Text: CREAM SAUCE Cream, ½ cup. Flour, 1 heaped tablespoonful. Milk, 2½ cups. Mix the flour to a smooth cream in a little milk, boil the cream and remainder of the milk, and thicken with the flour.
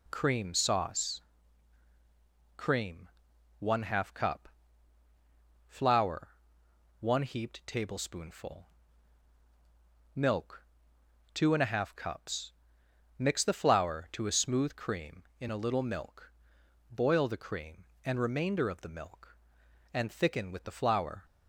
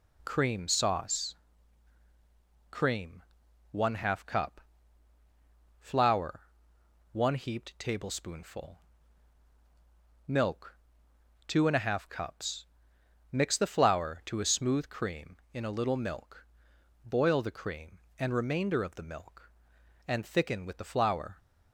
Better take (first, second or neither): neither